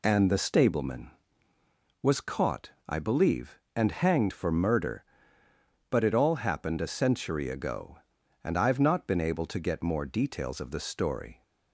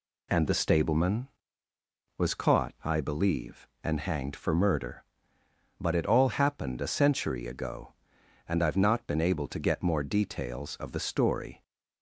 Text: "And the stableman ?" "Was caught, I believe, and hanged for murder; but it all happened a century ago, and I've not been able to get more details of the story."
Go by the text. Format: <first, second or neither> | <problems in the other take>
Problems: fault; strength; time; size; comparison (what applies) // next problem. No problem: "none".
neither | none